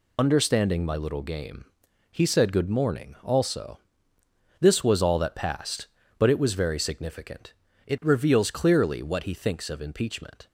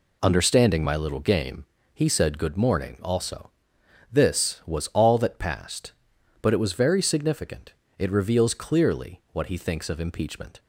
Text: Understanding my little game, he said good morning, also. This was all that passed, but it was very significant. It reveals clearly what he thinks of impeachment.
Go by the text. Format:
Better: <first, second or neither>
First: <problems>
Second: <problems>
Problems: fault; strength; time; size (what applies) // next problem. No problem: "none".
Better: second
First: loses the start of "Understanding"; at 0.1 s; 40 ms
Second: none